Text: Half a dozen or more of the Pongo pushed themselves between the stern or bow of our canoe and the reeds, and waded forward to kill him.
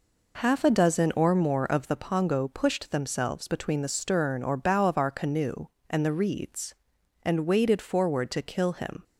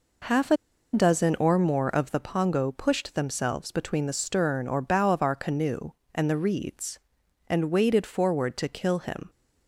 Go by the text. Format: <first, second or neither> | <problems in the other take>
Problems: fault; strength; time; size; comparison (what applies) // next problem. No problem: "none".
first | pauses between "a" and "dozen"; at 0.5 s; 0.37 s long